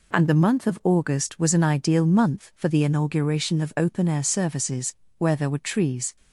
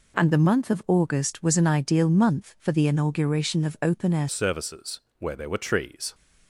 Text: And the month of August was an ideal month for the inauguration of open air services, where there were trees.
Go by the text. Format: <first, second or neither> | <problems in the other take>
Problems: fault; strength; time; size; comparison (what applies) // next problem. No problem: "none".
first | changes voice at "services"; from 4.2 s on; 1.9 s long